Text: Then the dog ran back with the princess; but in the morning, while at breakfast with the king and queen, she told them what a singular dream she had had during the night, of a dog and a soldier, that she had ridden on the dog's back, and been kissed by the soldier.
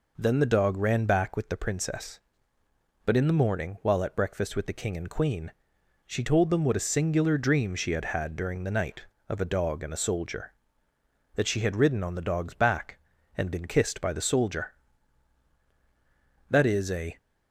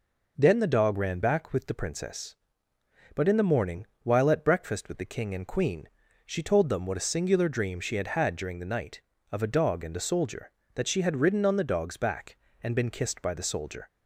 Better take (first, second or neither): second